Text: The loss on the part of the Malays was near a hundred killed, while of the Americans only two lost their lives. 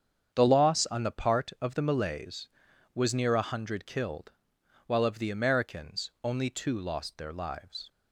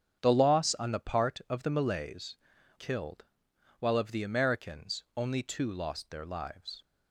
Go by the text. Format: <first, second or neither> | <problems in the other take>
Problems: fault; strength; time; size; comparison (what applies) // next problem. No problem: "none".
first | starts louder than the rest; strong; until 1.2 s; 8 dB; strong in the first // skips "was near a hundred"; at 2.5 s